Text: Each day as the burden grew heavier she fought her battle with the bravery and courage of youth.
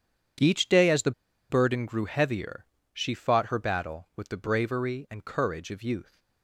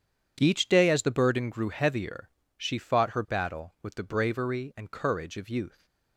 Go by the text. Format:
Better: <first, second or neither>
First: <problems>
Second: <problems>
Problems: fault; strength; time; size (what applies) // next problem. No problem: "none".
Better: second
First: starts louder than the rest; strong; until 1.8 s; 8.5 dB // pauses between "the" and "burden"; at 1.1 s; 0.38 s long // pauses between "heavier" and "she"; slight; at 2.6 s; 0.28 s long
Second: starts louder than the rest; strong; until 1.4 s; 8.5 dB // pauses between "heavier" and "she"; slight; at 2.2 s; 0.28 s long